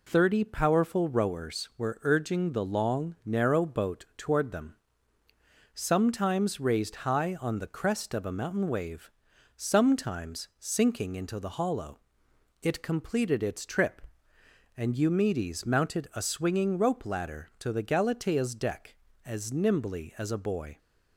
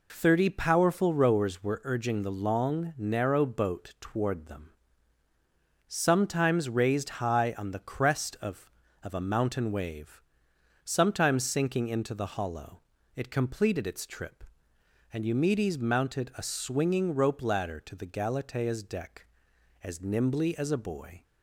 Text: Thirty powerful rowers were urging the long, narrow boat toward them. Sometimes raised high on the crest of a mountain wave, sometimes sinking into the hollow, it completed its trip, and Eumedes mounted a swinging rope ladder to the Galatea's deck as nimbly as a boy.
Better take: first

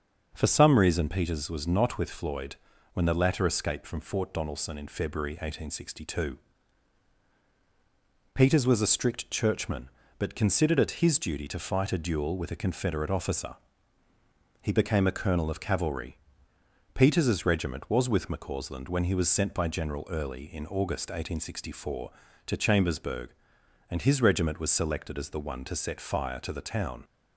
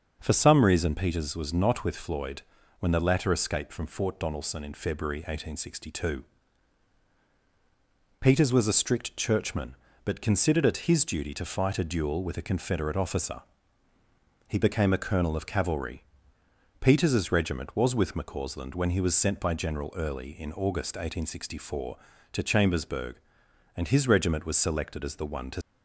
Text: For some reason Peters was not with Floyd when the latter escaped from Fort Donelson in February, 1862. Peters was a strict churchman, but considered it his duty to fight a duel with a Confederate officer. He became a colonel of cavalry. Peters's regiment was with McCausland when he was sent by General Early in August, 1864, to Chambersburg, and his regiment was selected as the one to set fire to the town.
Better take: first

